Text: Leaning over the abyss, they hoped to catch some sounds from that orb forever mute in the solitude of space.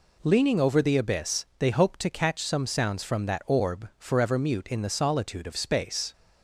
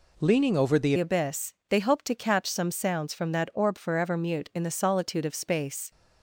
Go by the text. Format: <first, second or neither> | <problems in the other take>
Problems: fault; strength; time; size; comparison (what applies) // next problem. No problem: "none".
first | changes voice at "abyss"; from 0.9 s on; 5.0 s long